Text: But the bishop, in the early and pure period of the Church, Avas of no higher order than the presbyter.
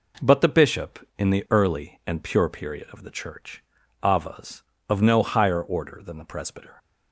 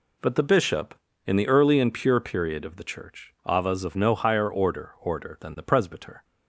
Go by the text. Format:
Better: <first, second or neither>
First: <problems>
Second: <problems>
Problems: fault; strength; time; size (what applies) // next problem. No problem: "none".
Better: first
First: none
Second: says "order" twice; at 5.0 s